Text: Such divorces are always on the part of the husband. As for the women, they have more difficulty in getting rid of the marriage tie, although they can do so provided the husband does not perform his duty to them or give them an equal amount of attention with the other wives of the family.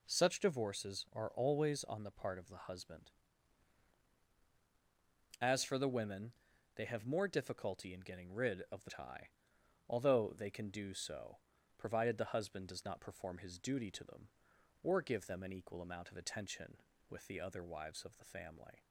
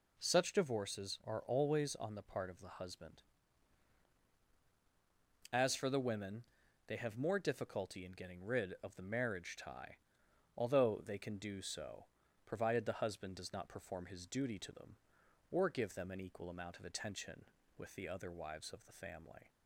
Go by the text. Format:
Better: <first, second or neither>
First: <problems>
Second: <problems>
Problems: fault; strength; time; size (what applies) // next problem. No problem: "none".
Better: second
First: skips "marriage"; at 8.8 s // pauses between "so" and "provided"; at 11.3 s; 0.40 s long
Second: pauses between "so" and "provided"; at 12.0 s; 0.40 s long